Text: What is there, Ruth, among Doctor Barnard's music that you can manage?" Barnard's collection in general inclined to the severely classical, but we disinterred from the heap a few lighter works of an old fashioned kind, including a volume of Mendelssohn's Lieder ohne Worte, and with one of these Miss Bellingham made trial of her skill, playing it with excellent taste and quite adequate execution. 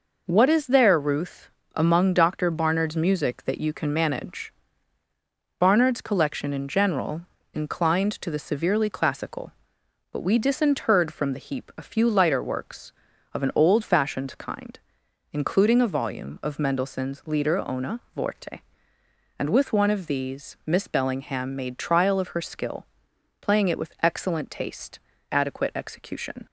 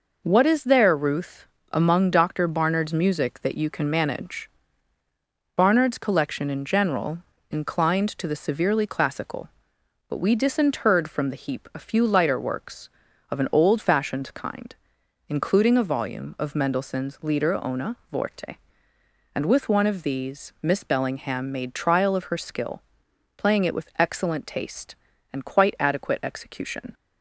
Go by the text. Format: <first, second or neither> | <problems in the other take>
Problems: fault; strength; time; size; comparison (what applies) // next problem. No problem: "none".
second | pauses between "general" and "inclined"; slight; at 7.2 s; 0.32 s long; slight in the second // pauses between "ohne" and "Worte"; slight; at 17.9 s; 0.16 s long; slight in the second // skips "and quite"; at 25.1 s